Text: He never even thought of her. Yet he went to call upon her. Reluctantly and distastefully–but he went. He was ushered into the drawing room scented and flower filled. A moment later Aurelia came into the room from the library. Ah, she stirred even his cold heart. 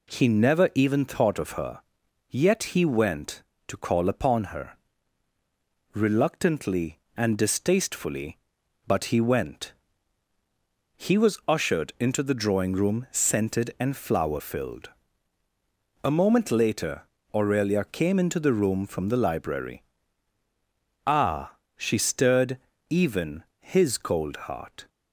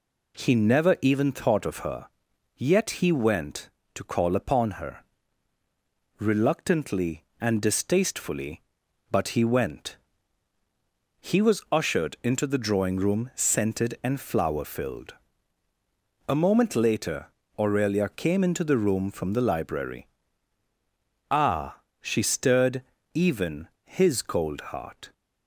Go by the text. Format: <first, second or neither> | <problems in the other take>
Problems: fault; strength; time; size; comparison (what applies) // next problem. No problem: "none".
neither | pauses between "later" and "Aurelia"; slight; the same in both // pauses between "stirred" and "even"; slight; the same in both // pauses between "even" and "his"; slight; the same in both